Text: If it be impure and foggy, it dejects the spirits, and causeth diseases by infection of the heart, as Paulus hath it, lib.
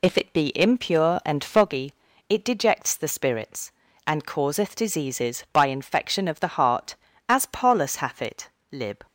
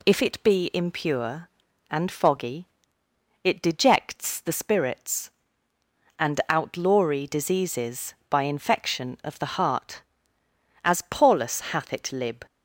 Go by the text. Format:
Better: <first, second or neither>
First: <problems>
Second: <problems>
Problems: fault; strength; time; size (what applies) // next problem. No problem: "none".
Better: first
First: none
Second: says "outlawry" for "causeth"; at 6.4 s